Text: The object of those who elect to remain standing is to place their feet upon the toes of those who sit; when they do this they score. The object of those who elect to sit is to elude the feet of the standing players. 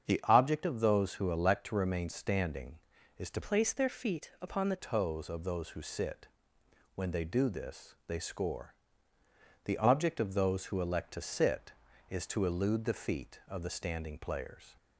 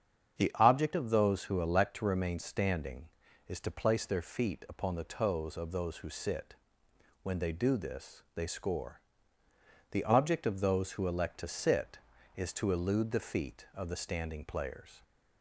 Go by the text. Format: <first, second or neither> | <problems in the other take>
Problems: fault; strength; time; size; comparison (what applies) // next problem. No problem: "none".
second | starts louder than the rest; strong; until 1.0 s; 7.5 dB; strong in the second // changes voice from "place" to "the"; from 3.4 to 4.7 s; 1.3 s long